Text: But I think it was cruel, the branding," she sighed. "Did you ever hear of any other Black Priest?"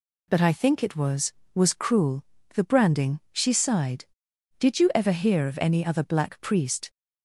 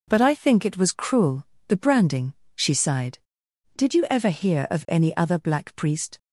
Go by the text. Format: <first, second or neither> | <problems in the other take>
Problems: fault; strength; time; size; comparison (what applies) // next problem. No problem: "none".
second | says "was" twice; at 1.5 s